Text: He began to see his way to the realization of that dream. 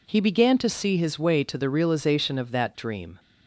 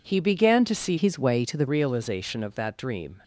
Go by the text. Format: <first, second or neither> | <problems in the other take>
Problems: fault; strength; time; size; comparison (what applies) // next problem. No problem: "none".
first | changes voice from "his" to "the"; from 0.9 to 1.6 s; 0.7 s long